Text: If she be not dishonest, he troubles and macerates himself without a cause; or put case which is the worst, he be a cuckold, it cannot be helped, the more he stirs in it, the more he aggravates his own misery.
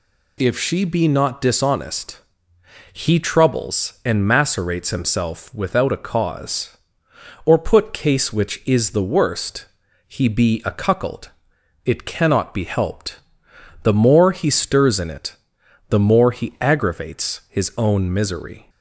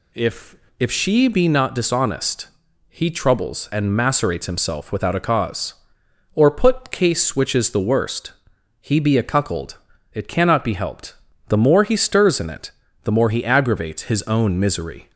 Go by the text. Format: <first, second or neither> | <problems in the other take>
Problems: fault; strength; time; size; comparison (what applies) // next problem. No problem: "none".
first | says "If" twice; at 0.7 s